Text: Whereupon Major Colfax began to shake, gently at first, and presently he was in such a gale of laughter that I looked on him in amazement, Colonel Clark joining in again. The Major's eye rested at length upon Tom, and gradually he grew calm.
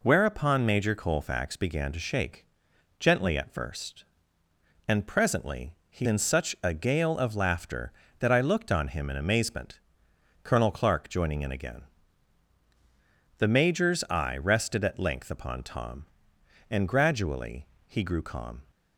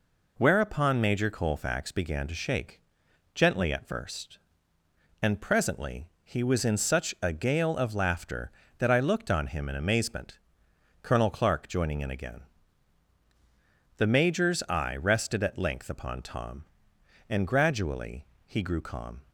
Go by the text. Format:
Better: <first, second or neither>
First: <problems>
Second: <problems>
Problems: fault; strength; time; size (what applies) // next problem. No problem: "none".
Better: second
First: pauses between "presently" and "he"; slight; at 5.7 s; 0.16 s long // skips "was"; at 6.0 s // pauses between "gradually" and "he"; slight; at 17.6 s; 0.20 s long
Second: pauses between "presently" and "he"; slight; at 6.0 s; 0.16 s long // pauses between "gradually" and "he"; slight; at 18.2 s; 0.20 s long